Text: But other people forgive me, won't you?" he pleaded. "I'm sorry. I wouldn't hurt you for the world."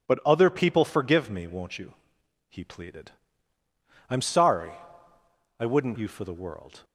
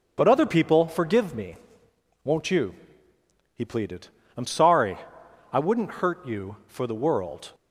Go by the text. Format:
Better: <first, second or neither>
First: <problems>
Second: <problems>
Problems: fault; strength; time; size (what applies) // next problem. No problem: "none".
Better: second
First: skips "hurt"; at 5.9 s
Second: none